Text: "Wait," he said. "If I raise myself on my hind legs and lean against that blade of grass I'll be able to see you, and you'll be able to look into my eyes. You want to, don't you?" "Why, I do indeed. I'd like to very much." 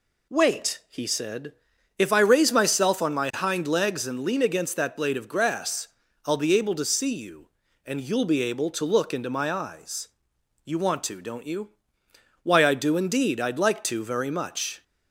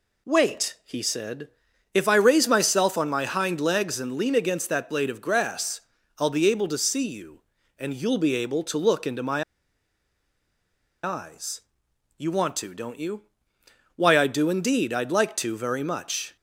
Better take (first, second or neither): first